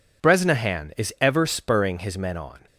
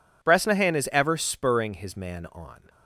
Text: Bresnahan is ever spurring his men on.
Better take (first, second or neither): first